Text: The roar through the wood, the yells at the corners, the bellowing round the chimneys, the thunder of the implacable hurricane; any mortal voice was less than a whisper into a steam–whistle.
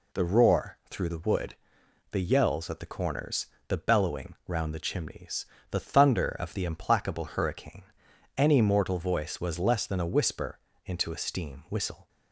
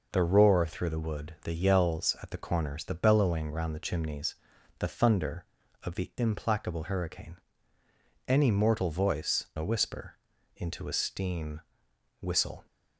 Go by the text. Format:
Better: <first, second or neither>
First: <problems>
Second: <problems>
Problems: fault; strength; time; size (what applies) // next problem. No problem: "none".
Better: first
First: pauses between "whisper" and "into"; slight; at 10.6 s; 0.26 s long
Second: skips "was less than"; at 9.5 s // pauses between "whisper" and "into"; at 10.1 s; 0.38 s long